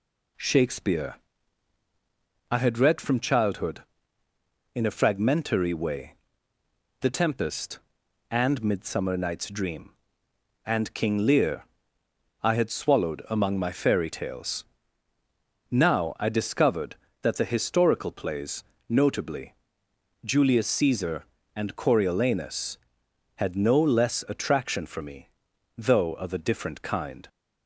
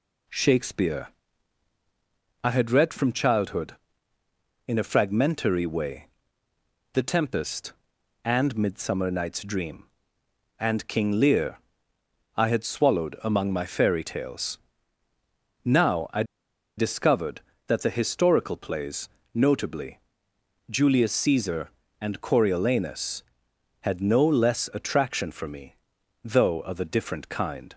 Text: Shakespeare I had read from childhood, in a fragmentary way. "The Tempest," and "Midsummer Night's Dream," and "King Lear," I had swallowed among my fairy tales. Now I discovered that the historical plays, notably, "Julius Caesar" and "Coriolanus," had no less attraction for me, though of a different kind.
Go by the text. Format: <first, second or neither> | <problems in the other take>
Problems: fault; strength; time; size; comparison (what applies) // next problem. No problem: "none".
first | pauses between "Shakespeare" and "I"; strong; at 1.0 s; 1.3 s long; strong in the first // pauses between "I" and "discovered"; noticeable; at 16.2 s; 0.54 s long